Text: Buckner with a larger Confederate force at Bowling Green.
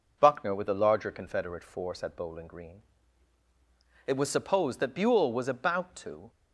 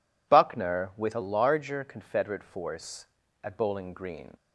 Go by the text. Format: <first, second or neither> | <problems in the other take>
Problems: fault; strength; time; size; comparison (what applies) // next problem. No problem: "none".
second | goes on to say "It was supposed that Buell was about to"; strong; from 4.0 s on; 2.2 s long